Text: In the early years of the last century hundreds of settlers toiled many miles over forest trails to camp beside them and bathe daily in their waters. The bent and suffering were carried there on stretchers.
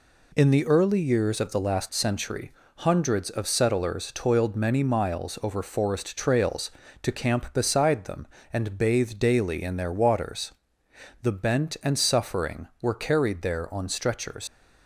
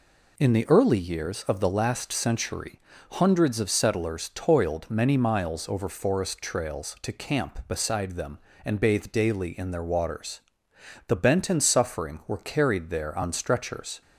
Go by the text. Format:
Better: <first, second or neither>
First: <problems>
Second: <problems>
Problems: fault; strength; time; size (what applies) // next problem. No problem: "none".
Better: second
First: pauses between "century" and "hundreds"; slight; at 2.5 s; 0.28 s long // leaves "stretchers" unfinished; at 14.4 s; 85 ms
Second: pauses between "century" and "hundreds"; slight; at 2.7 s; 0.34 s long